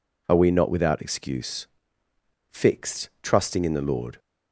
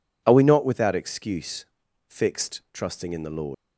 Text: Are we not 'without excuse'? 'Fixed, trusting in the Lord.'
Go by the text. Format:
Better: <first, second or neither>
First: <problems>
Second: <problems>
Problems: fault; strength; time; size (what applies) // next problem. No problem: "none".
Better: first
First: none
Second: leaves "Lord" unfinished; at 3.5 s; 105 ms